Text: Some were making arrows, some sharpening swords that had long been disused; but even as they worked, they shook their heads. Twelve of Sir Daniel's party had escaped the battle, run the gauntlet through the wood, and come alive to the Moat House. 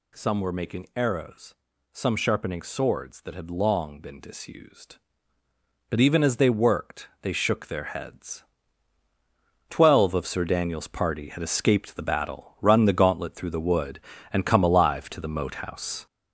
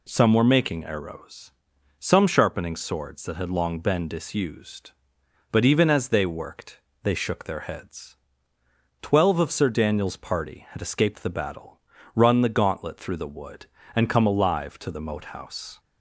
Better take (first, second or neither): second